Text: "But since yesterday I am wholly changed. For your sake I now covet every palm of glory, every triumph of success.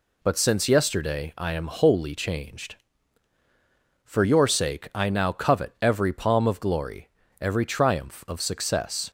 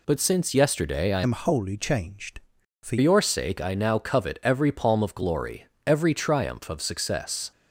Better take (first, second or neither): first